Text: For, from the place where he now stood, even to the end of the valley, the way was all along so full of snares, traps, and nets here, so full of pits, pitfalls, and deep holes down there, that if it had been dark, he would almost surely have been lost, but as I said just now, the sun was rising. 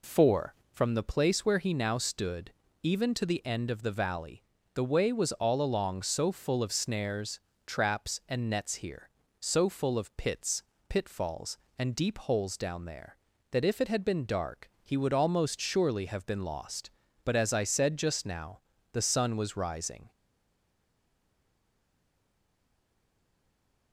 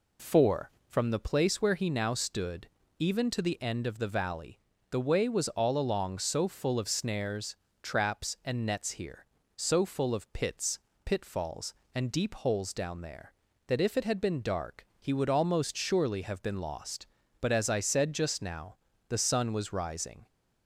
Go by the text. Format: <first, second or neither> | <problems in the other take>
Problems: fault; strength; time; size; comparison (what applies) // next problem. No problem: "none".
second | stays silent after the last word; strong; from 20.1 s on; 3.8 s long